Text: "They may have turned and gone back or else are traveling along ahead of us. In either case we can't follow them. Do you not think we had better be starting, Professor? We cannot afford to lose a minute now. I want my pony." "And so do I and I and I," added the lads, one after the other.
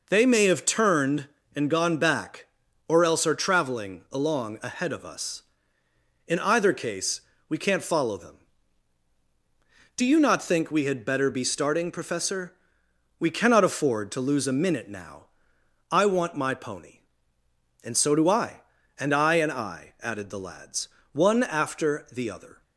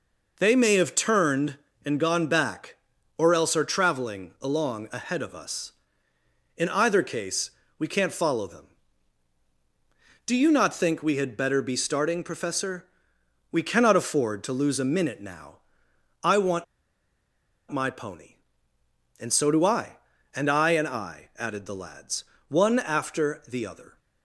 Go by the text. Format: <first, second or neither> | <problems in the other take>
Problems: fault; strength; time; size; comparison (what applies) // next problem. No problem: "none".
first | pauses between "case" and "we"; slight; at 7.5 s; 0.28 s long; slight in the first // pauses between "want" and "my"; at 16.6 s; 1.0 s long